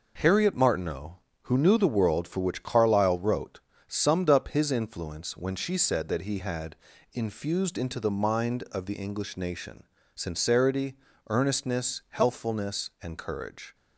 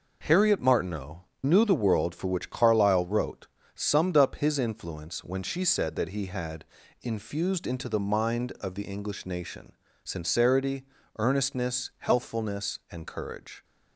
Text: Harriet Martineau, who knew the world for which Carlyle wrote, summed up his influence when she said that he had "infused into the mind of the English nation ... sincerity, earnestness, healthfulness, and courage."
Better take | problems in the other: first | skips "who"; at 1.3 s // pauses between "had" and "infused"; slight; at 6.6 s; 0.36 s long; slight in the first

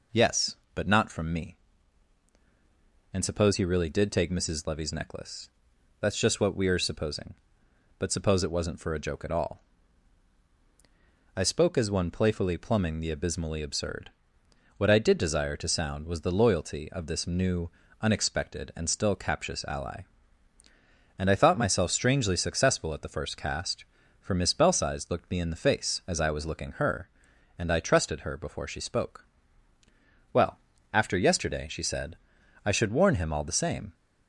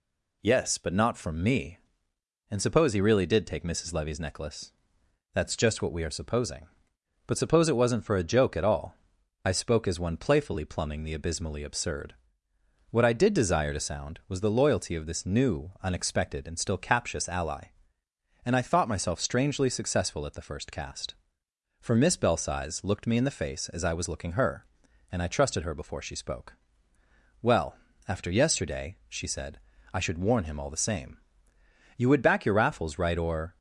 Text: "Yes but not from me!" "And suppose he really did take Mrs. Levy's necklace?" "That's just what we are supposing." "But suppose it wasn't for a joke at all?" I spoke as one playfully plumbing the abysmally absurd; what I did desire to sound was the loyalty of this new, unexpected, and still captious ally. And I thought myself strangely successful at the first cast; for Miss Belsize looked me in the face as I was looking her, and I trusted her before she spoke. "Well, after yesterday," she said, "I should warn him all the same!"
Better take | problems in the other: first | goes on to say "You would back your Raffles right or"; from 31.9 s on; 1.6 s long

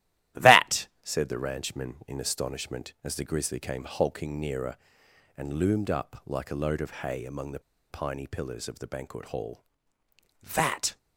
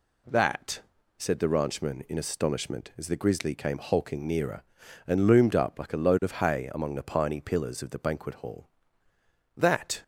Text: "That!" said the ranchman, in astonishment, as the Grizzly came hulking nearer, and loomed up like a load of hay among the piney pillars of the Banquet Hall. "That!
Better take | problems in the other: second | starts louder than the rest; strong; until 1.5 s; 14.5 dB // pauses between "the" and "piney"; slight; at 7.5 s; 0.30 s long

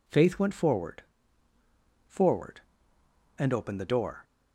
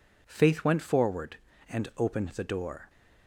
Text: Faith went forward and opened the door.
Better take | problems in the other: second | says "forward" twice; at 2.0 s

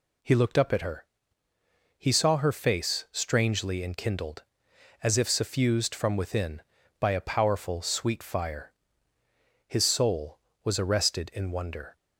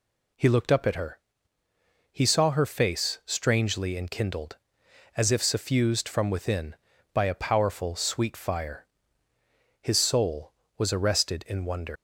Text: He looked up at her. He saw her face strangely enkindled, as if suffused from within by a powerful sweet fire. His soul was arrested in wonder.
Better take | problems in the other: first | leaves "wonder" unfinished; at 11.9 s; 140 ms

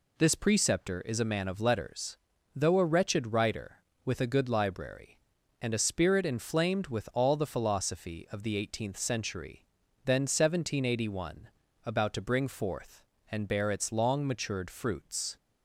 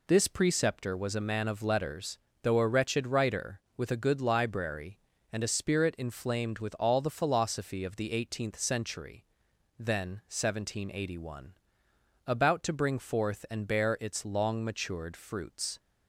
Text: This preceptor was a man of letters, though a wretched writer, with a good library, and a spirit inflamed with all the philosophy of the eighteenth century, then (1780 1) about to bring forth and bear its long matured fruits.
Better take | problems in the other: second | says "is" for "was"; at 1.0 s

